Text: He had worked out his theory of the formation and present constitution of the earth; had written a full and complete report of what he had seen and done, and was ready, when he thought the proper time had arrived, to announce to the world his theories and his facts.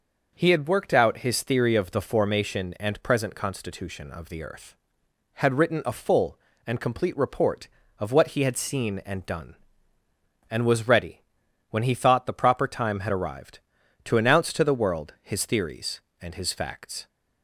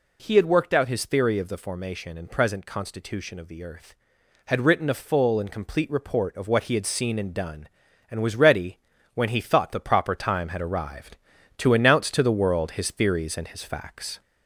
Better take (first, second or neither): first